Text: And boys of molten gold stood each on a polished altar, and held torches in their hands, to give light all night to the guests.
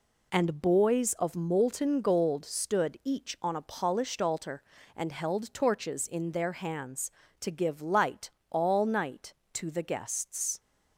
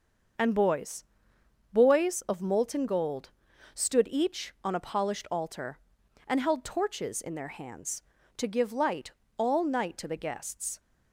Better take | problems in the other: first | starts louder than the rest; until 2.0 s; 6.5 dB // says "boys" twice; at 1.7 s // pauses between "gold" and "stood"; at 3.2 s; 0.44 s long // pauses between "light" and "all"; slight; at 9.1 s; 0.26 s long; slight in the first

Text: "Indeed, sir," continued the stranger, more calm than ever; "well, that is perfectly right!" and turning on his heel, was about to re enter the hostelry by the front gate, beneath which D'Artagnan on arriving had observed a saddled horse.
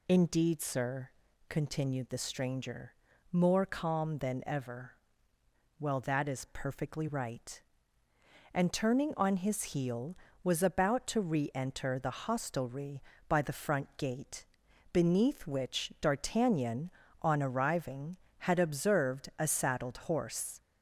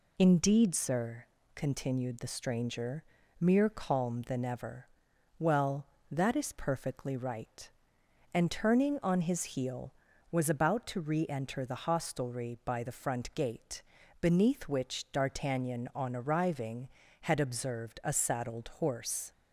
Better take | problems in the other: first | says "mere" for "more"; at 3.4 s

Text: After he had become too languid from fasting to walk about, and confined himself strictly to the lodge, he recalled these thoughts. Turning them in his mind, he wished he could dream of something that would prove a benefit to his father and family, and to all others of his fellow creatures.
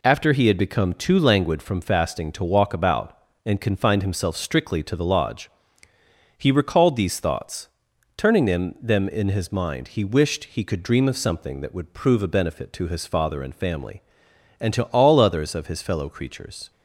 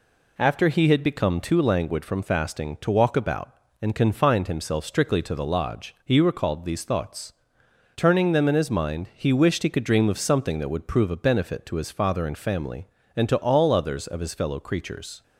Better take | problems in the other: second | says "them" twice; at 8.8 s

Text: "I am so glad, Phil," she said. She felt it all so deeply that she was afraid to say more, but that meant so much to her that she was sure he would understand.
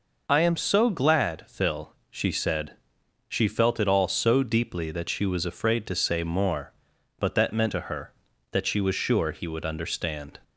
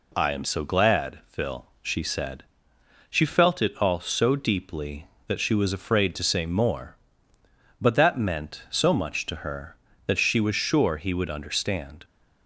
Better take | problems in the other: second | skips "so much"; at 7.7 s

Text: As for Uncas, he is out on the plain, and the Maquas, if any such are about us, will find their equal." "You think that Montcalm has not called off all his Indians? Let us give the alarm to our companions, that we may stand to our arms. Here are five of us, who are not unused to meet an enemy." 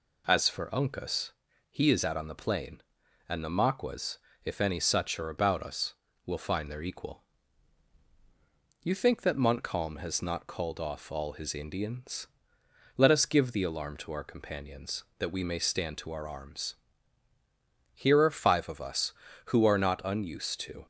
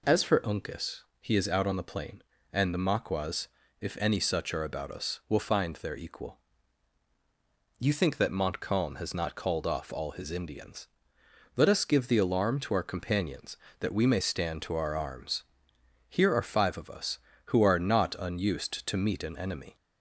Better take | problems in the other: second | stops before "meet an enemy"; at 20.8 s

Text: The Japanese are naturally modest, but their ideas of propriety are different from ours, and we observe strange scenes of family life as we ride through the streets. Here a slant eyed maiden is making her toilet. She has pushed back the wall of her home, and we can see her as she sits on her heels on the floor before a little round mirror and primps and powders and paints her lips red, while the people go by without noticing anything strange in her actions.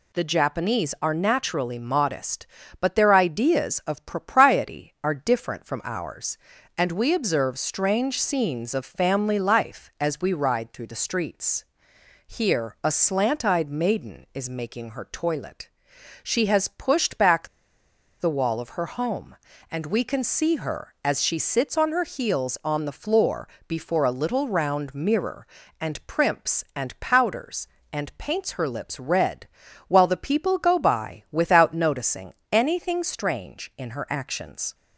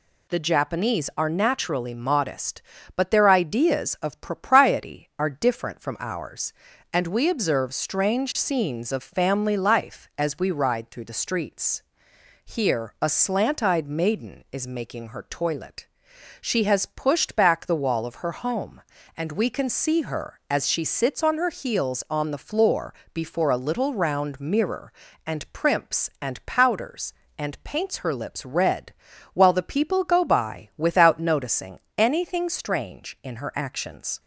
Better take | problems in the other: second | pauses between "back" and "the"; noticeable; at 17.4 s; 0.73 s long // pauses between "floor" and "before"; slight; at 23.4 s; 0.22 s long; slight in the second // pauses between "noticing" and "anything"; slight; at 32.3 s; 0.18 s long; slight in the second

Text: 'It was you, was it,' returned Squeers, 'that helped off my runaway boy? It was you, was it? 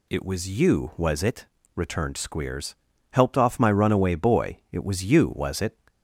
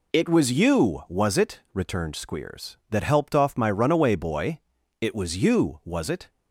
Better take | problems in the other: second | skips "that"; at 2.9 s

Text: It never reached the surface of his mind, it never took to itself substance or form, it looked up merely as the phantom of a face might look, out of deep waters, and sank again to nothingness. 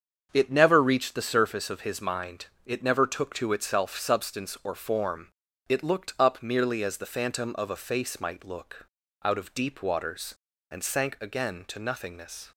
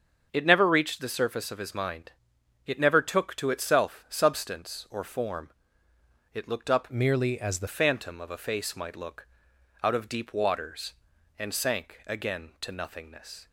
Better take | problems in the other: first | starts louder than the rest; strong; until 1.3 s; 7 dB; also in the first // changes voice from "merely" to "the"; from 6.8 to 7.6 s; 0.8 s long

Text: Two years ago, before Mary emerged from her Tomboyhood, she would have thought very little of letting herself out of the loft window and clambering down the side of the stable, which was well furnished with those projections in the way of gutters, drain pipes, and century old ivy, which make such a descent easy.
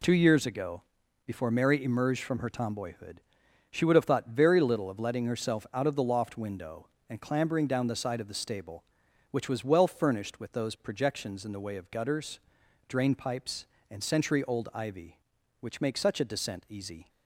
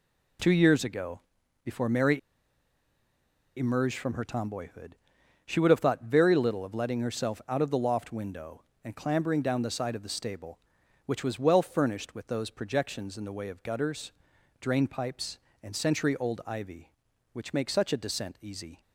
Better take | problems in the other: first | pauses between "Mary" and "emerged"; strong; at 2.1 s; 1.3 s long

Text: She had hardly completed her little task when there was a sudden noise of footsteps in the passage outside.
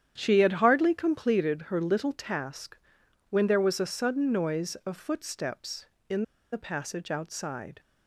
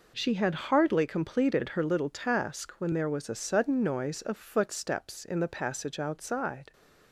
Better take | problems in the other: second | starts louder than the rest; strong; until 1.1 s; 9.5 dB // pauses between "task" and "when"; noticeable; at 2.7 s; 0.50 s long // pauses between "in" and "the"; slight; at 6.2 s; 0.30 s long

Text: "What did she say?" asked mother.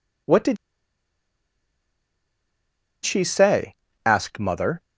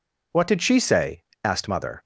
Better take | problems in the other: second | pauses between "did" and "she"; strong; at 0.5 s; 2.4 s long

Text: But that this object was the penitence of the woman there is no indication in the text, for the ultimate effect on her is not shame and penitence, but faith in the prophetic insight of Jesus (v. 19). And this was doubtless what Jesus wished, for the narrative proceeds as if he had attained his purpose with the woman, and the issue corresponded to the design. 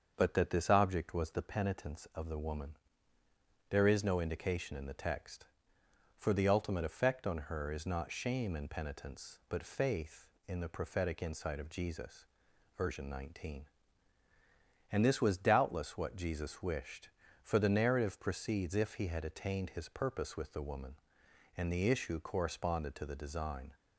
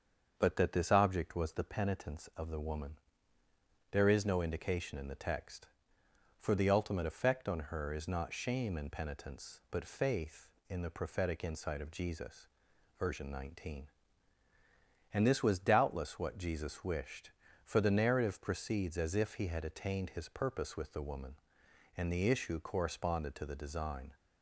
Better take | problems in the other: second | starts louder than the rest; until 1.1 s; 6.5 dB; also in the second // pauses between "woman" and "there"; noticeable; at 2.7 s; 0.94 s long; noticeable in the second // skips "as"; at 18.7 s

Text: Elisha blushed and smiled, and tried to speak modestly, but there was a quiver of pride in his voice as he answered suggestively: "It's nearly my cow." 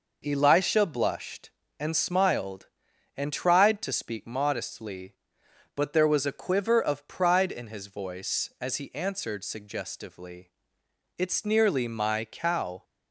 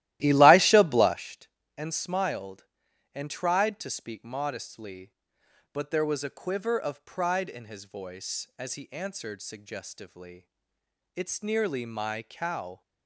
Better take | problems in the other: first | starts louder than the rest; strong; until 1.3 s; 15 dB

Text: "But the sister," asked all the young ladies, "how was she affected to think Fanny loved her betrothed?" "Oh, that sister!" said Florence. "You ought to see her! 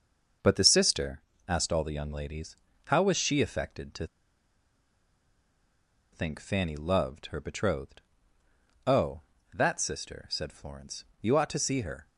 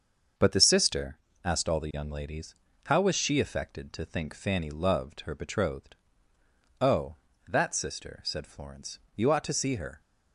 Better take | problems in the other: second | starts louder than the rest; until 1.6 s; 6.5 dB; also in the second // pauses between "to" and "think"; strong; at 4.0 s; 2.0 s long

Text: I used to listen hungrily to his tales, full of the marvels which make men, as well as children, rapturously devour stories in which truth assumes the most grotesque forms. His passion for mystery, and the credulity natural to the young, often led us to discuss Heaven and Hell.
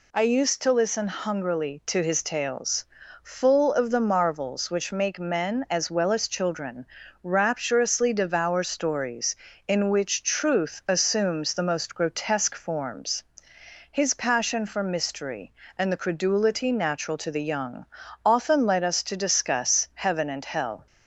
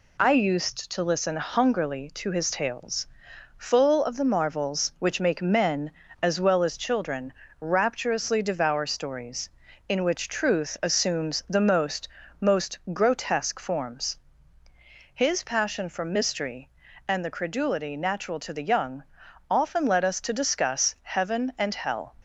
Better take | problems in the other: first | says "most" twice; at 12.3 s

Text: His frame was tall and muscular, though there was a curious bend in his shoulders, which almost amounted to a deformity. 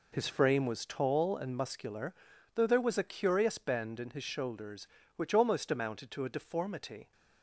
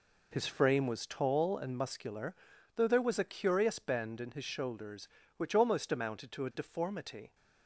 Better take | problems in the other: neither | none

